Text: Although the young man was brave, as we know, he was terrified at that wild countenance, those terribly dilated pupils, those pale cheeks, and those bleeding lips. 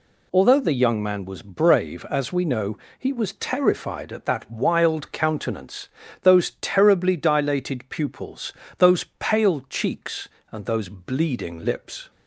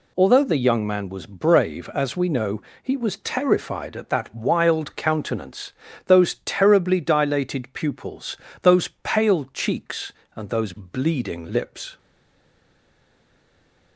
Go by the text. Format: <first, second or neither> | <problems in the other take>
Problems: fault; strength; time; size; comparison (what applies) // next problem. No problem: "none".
first | stays silent after the last word; noticeable; from 11.9 s on; 2.0 s long